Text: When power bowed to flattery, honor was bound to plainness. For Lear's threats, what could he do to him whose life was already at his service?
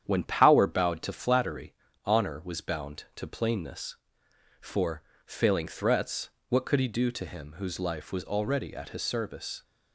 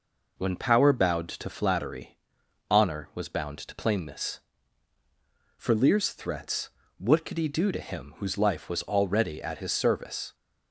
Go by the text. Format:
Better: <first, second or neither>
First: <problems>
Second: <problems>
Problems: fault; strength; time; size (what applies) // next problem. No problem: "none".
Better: second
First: starts louder than the rest; strong; until 1.0 s; 9 dB // says "Failing" for "Lear's"; at 5.2 s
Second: none